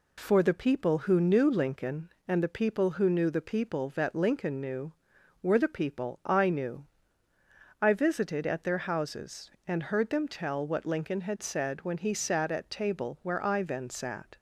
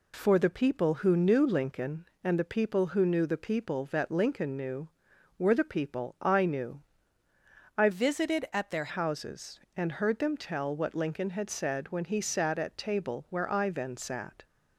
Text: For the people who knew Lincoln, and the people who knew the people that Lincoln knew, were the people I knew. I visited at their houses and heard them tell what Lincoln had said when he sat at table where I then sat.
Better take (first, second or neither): first